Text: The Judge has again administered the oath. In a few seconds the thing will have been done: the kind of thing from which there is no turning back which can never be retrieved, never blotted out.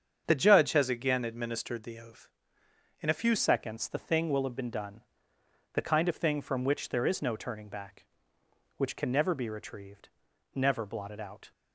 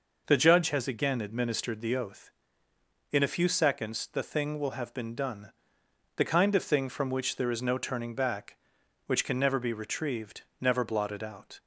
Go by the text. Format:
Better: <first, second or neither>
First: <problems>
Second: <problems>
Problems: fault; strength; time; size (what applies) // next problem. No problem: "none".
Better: second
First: starts louder than the rest; strong; until 1.2 s; 7.5 dB // changes voice at "seconds"; from 3.3 s on; 8.2 s long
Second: none